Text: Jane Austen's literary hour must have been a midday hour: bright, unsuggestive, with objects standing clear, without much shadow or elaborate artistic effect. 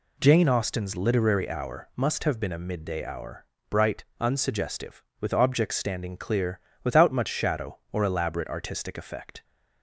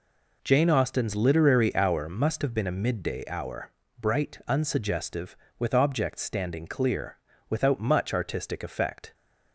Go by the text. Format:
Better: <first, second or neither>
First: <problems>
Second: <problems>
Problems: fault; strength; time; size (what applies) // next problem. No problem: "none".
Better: first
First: none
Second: skips "shadow or elaborate"; at 8.1 s